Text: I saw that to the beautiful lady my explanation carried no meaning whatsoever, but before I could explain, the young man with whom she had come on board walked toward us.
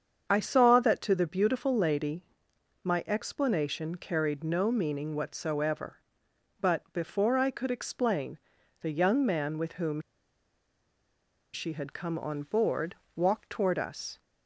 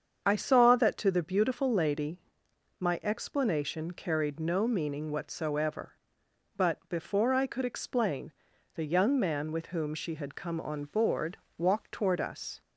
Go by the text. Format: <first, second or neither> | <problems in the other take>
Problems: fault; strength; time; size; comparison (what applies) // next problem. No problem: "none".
second | starts louder than the rest; strong; until 1.2 s; 7.5 dB; strong in the second // pauses between "lady" and "my"; noticeable; at 2.2 s; 0.60 s long; noticeable in the second // pauses between "whom" and "she"; strong; at 10.0 s; 1.5 s long // pauses between "board" and "walked"; slight; at 12.9 s; 0.20 s long; slight in the second